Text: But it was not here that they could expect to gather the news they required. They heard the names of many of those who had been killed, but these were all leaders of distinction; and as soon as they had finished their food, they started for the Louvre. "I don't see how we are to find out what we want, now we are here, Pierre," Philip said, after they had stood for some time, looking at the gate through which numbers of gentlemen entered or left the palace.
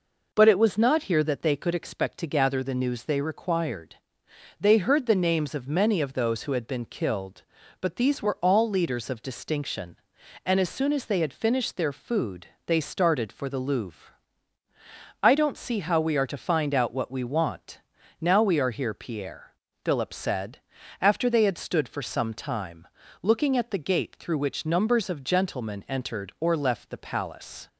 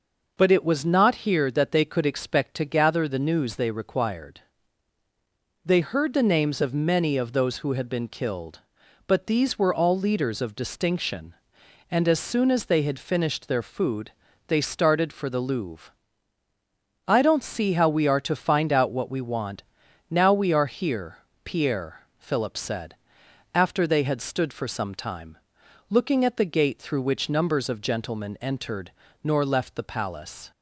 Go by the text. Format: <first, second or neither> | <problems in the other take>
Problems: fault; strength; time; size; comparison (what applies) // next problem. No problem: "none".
first | says "nor" for "or"; at 29.2 s